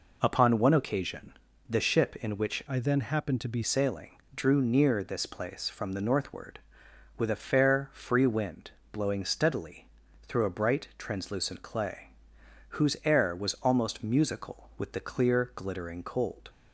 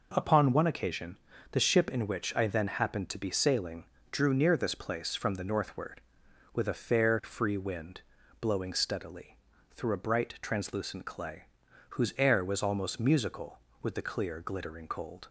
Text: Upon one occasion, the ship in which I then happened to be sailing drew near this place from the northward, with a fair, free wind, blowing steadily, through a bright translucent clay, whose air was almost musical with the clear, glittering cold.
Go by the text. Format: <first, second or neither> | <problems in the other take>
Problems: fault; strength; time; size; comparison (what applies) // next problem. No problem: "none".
second | changes voice from "I" to "be"; from 2.6 to 3.6 s; 1.0 s long // pauses between "sailing" and "drew"; slight; at 4.1 s; 0.24 s long; slight in the second